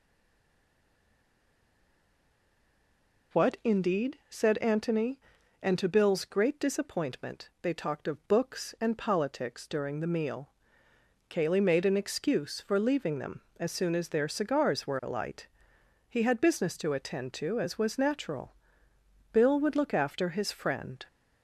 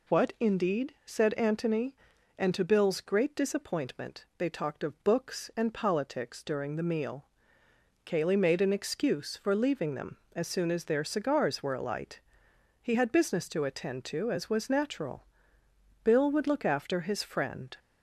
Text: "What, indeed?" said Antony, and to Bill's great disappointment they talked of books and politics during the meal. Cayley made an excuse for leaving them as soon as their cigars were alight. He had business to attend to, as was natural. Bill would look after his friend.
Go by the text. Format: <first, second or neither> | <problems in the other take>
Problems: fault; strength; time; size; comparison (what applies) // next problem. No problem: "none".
second | stays silent before the first word; strong; until 3.3 s; 3.3 s long